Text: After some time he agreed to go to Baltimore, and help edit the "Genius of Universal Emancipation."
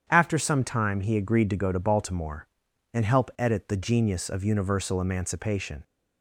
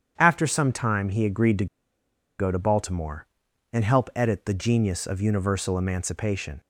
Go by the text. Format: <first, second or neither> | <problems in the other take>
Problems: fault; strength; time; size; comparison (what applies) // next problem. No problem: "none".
first | starts louder than the rest; strong; until 1.1 s; 8.5 dB; strong in the first // pauses between "to" and "go"; noticeable; at 1.6 s; 0.73 s long